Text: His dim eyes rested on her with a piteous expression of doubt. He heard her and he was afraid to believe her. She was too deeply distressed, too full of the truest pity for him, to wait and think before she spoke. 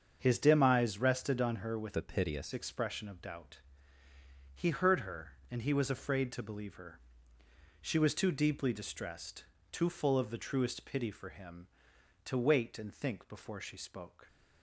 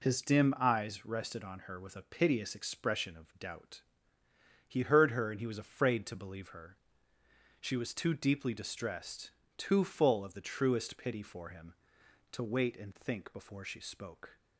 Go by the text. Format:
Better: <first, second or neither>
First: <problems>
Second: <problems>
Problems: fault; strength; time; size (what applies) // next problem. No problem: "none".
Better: second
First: starts louder than the rest; until 1.2 s; 7 dB // changes voice from "a" to "piteous"; from 1.9 to 2.5 s; 0.6 s long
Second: none